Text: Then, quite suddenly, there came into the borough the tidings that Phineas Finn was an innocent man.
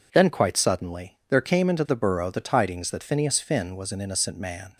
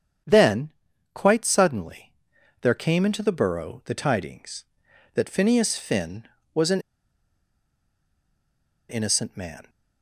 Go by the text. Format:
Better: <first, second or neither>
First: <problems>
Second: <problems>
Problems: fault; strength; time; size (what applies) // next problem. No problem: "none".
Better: first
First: none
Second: starts louder than the rest; strong; until 1.6 s; 8.5 dB // pauses between "an" and "innocent"; strong; at 6.8 s; 2.0 s long